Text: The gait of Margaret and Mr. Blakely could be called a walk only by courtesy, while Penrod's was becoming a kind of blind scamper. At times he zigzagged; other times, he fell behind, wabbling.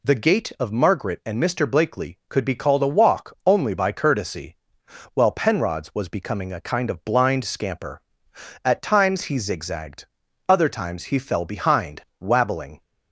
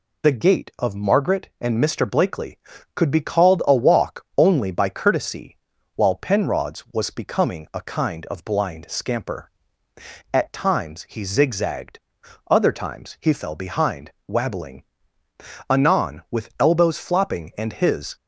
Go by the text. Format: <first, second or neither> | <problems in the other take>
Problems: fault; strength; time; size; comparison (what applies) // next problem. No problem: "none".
first | goes on to say "Anon with elbows flopping and his"; strong; from 15.6 s on; 2.4 s long